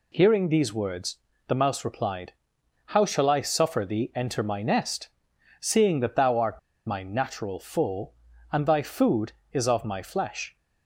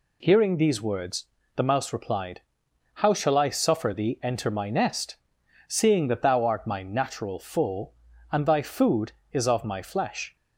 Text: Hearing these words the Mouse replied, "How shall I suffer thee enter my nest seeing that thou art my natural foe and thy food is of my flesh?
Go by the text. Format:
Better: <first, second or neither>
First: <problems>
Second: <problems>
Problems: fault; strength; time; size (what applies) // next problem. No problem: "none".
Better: second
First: pauses between "words" and "the"; slight; at 1.1 s; 0.30 s long // pauses between "nest" and "seeing"; noticeable; at 5.0 s; 0.50 s long // pauses between "art" and "my"; slight; at 6.5 s; 0.28 s long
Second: pauses between "words" and "the"; slight; at 1.2 s; 0.30 s long // pauses between "nest" and "seeing"; noticeable; at 5.1 s; 0.50 s long